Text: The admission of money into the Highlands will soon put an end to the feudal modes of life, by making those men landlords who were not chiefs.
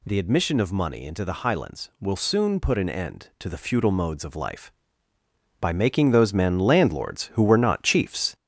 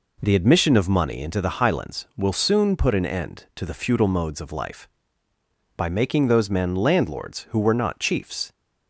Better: second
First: gets louder; noticeable; throughout; 4.5 dB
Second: none

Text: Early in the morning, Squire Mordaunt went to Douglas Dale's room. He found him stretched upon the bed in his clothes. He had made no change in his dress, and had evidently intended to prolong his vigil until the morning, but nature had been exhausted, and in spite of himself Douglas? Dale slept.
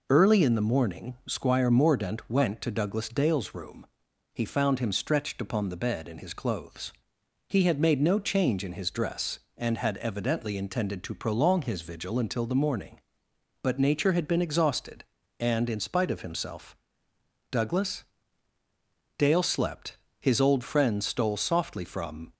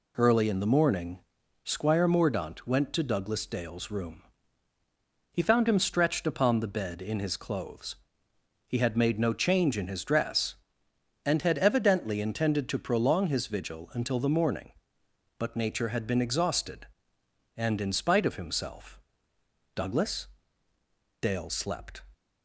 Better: second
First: pauses between "himself" and "Douglas"; noticeable; at 16.7 s; 0.76 s long // goes on to say "His old friend stole softly from"; strong; from 20.1 s on; 2.1 s long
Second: pauses between "himself" and "Douglas"; noticeable; at 18.9 s; 0.76 s long

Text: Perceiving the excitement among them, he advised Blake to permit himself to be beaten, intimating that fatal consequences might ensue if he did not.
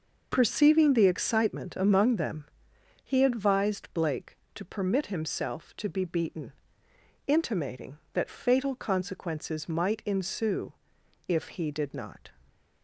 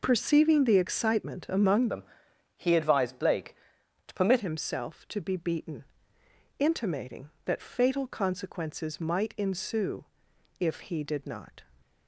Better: first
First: pauses between "ensue" and "if"; noticeable; at 10.7 s; 0.56 s long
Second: changes voice from "them" to "permit"; from 1.8 to 4.3 s; 2.5 s long // pauses between "ensue" and "if"; noticeable; at 10.0 s; 0.56 s long

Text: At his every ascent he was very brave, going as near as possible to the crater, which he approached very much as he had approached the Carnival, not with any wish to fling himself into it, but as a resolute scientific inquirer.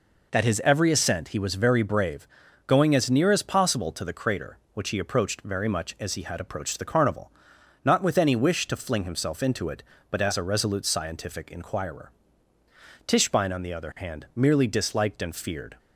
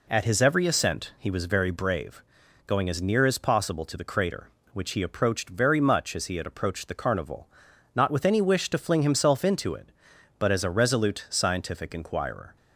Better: second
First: goes on to say "Tischbein on the other hand merely disliked and feared"; strong; from 13.0 s on; 2.7 s long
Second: none

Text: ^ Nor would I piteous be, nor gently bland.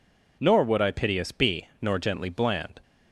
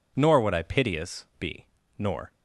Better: first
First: none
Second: stops before "gently bland"; at 2.3 s

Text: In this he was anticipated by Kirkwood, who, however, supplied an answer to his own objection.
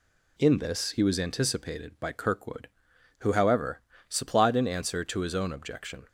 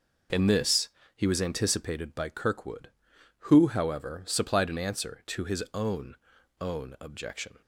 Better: first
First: none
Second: pauses between "this" and "he"; slight; at 0.8 s; 0.30 s long // says "own" twice; at 6.6 s

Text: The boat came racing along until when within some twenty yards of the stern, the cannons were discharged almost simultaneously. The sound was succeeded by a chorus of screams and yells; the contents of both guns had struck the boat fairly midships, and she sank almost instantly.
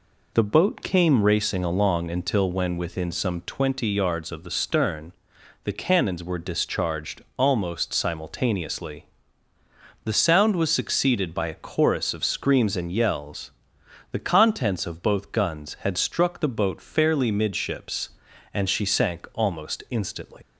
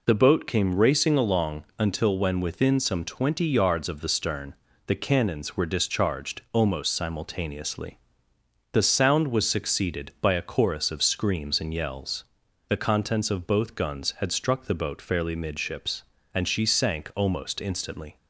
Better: second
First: leaves "instantly" unfinished; at 20.4 s; 125 ms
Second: none

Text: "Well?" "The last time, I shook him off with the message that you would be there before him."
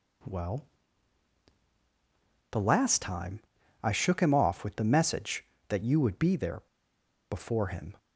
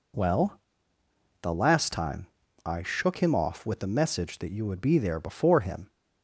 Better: second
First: pauses between "there" and "before"; noticeable; at 6.6 s; 0.68 s long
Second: none

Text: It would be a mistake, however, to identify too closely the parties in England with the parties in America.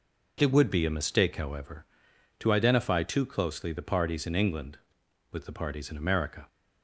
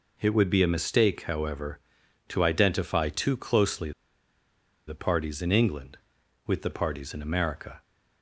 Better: first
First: none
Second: pauses between "closely" and "the"; noticeable; at 3.9 s; 0.96 s long

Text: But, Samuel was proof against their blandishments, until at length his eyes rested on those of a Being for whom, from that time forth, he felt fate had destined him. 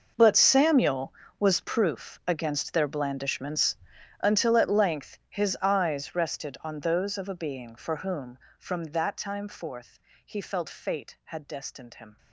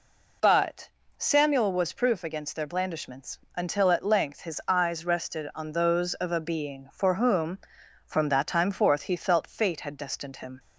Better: second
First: gets quieter; strong; throughout; 16.5 dB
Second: none

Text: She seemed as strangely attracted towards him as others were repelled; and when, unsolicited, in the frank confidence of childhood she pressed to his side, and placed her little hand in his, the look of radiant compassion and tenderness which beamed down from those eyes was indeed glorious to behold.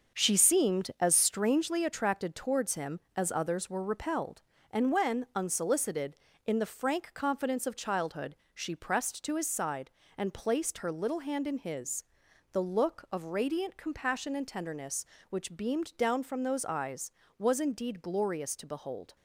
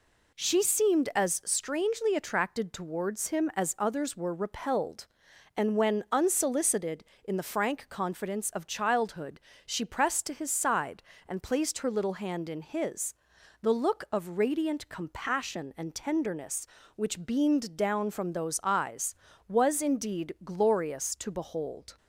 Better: second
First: gets quieter; strong; throughout; 7 dB // pauses between "childhood" and "she"; slight; at 8.3 s; 0.18 s long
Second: pauses between "childhood" and "she"; slight; at 9.3 s; 0.28 s long

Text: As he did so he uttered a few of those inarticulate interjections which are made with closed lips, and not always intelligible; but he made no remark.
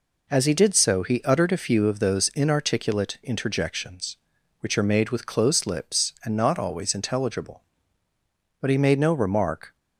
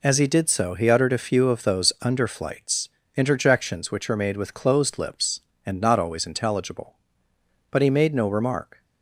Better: first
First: none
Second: says "underflights" for "inarticulate"; at 2.0 s

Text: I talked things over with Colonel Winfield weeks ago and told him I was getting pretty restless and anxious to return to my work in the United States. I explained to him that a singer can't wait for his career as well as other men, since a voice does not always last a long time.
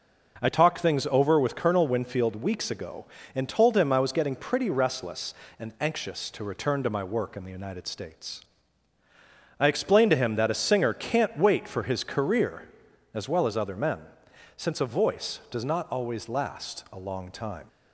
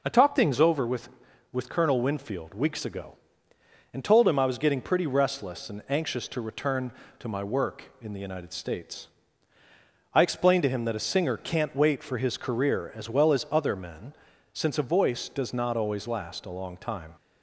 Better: first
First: none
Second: says "with" twice; at 1.5 s

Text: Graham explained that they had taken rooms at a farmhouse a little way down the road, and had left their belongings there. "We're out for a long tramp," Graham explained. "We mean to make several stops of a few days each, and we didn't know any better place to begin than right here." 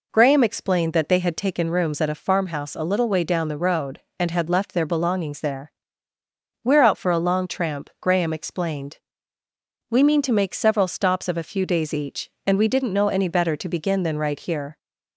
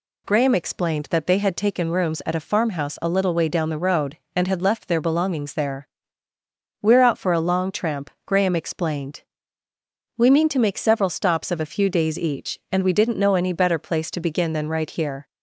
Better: second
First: skips "place"; at 13.5 s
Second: none

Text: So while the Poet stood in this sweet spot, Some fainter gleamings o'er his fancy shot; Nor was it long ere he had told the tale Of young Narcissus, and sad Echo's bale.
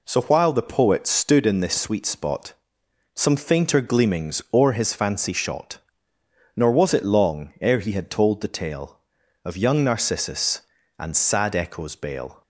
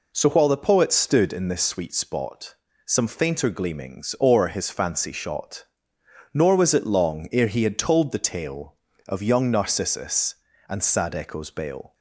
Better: neither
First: none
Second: none

